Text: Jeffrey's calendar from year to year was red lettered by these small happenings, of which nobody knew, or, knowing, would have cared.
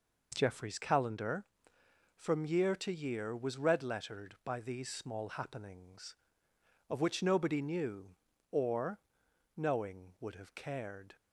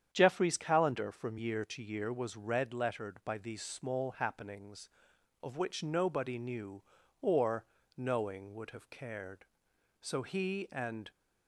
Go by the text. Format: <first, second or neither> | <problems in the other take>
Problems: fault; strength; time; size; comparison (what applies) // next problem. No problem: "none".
first | starts louder than the rest; strong; until 1.1 s; 8.5 dB // goes on to say "So he and"; noticeable; from 10.0 s on; 1.1 s long